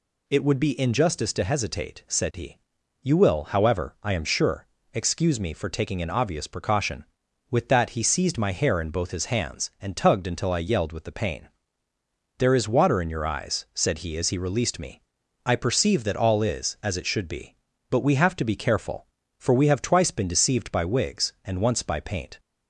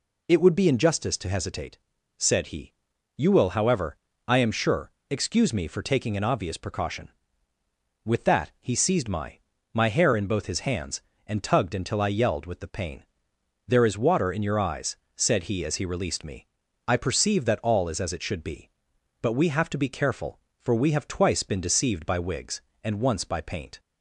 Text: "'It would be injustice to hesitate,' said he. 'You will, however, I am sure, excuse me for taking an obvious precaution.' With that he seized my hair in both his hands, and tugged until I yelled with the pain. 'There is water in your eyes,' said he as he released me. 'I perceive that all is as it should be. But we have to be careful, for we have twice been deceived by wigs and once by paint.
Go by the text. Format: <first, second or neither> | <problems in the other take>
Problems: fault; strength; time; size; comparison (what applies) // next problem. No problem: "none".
first | says "my" twice; at 9.7 s